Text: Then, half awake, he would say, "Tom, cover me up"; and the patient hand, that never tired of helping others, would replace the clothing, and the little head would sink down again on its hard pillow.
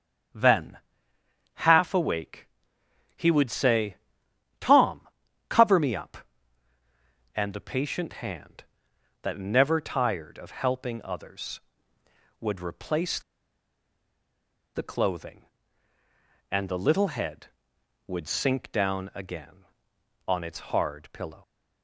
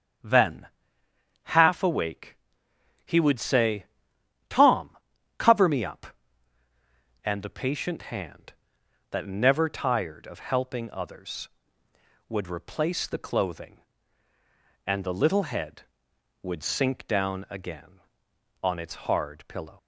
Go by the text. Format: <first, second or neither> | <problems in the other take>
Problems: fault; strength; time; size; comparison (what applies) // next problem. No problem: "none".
second | starts louder than the rest; strong; until 2.1 s; 8.5 dB; strong in the second // pauses between "replace" and "the"; strong; at 13.1 s; 1.5 s long // pauses between "its" and "hard"; slight; at 20.5 s; 0.16 s long; slight in the second